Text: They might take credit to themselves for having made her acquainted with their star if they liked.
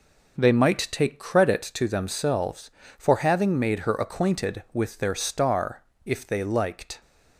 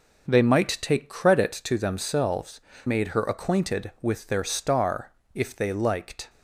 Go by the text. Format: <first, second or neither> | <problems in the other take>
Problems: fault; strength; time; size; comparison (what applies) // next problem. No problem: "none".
first | skips "for having"; at 2.7 s // pauses between "star" and "if"; slight; at 5.1 s; 0.22 s long; slight in the first